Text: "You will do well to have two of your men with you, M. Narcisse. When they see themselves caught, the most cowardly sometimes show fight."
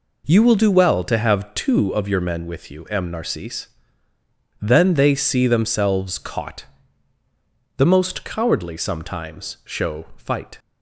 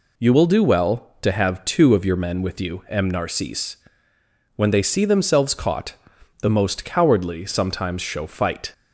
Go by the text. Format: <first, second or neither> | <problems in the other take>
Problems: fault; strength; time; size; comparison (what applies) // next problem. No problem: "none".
second | says "Then" for "When"; at 4.6 s